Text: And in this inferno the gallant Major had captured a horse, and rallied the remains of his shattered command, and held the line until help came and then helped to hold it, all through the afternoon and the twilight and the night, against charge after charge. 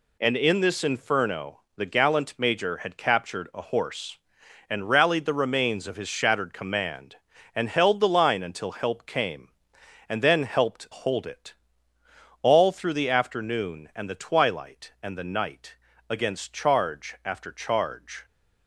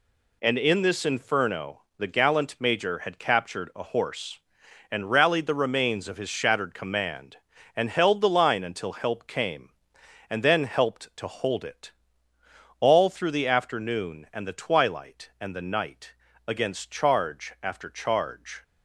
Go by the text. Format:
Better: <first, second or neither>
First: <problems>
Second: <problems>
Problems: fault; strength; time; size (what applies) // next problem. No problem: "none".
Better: second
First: pauses between "inferno" and "the"; slight; at 1.5 s; 0.16 s long // skips "to"; at 10.8 s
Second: pauses between "inferno" and "the"; slight; at 1.8 s; 0.16 s long